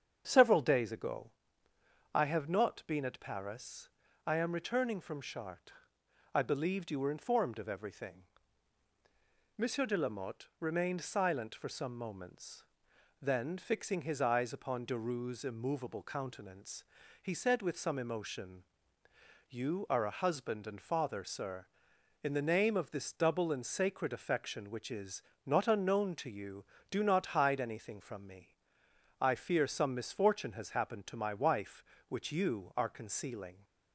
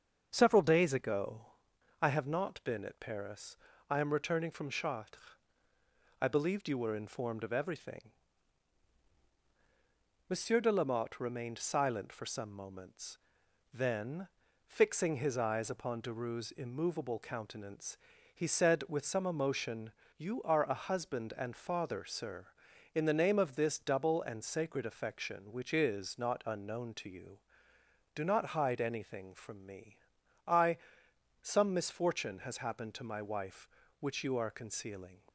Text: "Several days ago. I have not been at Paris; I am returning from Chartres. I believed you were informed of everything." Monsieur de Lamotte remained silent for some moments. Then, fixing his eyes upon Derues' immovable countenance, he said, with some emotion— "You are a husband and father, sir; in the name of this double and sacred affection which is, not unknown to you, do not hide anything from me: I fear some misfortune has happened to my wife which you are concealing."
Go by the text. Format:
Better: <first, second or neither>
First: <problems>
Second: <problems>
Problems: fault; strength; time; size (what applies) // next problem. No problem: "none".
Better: first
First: starts louder than the rest; strong; until 1.2 s; 7.5 dB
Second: starts louder than the rest; until 1.3 s; 7 dB // skips "fear"; at 31.0 s